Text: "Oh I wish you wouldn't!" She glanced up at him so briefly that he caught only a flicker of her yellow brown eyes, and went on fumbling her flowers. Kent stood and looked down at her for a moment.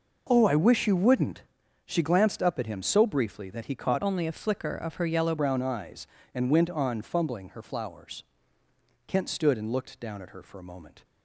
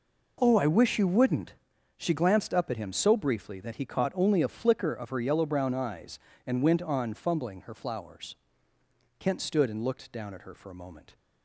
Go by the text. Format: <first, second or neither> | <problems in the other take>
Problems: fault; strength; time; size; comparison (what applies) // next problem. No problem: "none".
second | changes voice from "only" to "yellow"; from 4.0 to 5.3 s; 1.3 s long